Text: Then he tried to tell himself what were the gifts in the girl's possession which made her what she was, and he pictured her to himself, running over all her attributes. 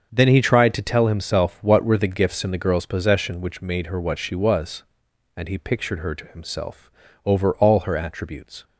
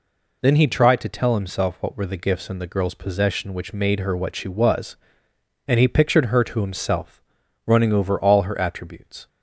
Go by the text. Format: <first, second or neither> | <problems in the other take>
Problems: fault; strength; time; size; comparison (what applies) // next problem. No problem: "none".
second | starts louder than the rest; until 1.1 s; 6.5 dB // skips "running"; at 7.0 s